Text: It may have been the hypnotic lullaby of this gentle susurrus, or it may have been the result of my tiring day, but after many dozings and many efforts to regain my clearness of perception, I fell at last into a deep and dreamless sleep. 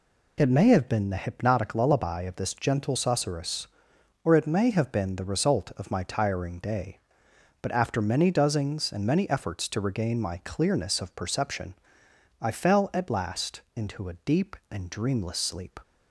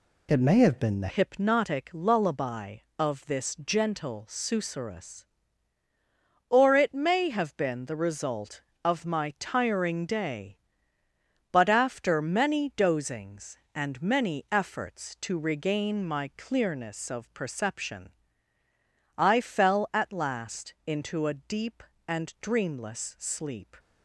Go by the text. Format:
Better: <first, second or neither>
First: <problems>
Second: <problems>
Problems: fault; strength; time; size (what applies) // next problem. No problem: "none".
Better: first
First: none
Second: changes voice at "hypnotic"; from 1.0 s on; 22.7 s long